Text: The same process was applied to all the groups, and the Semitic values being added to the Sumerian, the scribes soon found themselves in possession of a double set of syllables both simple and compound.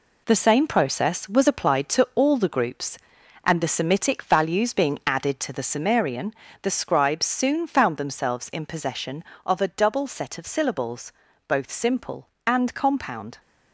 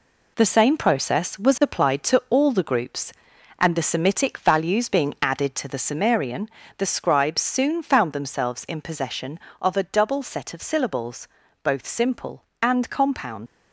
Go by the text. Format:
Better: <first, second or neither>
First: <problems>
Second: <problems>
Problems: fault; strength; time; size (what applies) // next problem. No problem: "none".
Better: first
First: pauses between "syllables" and "both"; slight; at 11.1 s; 0.36 s long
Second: pauses between "syllables" and "both"; slight; at 11.2 s; 0.36 s long // leaves "compound" unfinished; at 13.4 s; 90 ms